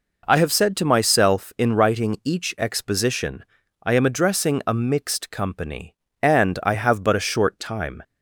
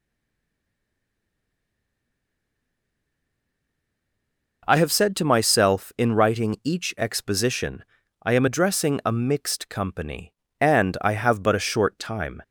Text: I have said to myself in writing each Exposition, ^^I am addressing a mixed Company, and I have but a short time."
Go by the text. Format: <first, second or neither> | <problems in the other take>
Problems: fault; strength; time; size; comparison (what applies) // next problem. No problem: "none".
first | stays silent before the first word; strong; until 4.6 s; 4.6 s long